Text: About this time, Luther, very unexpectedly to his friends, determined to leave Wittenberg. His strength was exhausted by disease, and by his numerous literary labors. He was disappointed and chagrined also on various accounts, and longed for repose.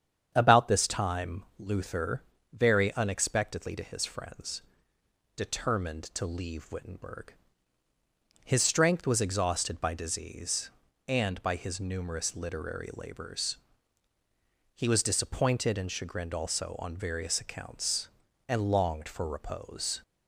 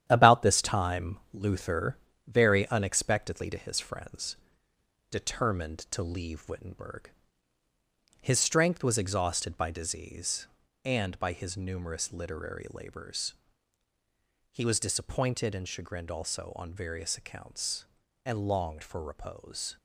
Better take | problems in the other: first | gets quieter; throughout; 6.5 dB // starts louder than the rest; strong; until 1.0 s; 10.5 dB; strong in the first

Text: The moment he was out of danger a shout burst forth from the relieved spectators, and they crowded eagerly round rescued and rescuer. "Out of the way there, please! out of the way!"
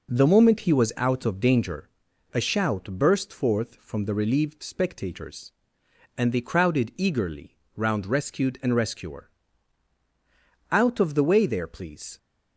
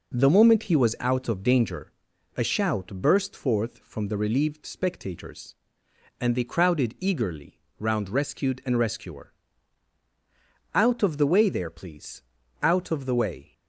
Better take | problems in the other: second | pauses between "danger" and "a"; noticeable; at 1.8 s; 0.46 s long; noticeable in the second // pauses between "eagerly" and "round"; slight; at 7.5 s; 0.20 s long; slight in the second // stops before "out of the way"; at 12.1 s

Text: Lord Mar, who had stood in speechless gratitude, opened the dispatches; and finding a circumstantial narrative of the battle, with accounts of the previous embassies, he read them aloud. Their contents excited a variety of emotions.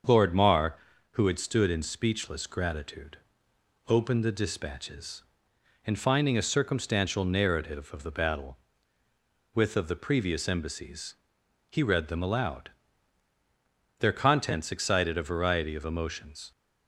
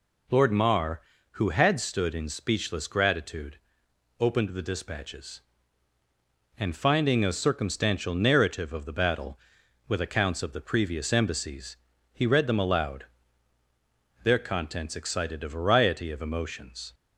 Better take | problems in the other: second | starts louder than the rest; until 1.4 s; 6.5 dB // skips "accounts"; at 9.7 s

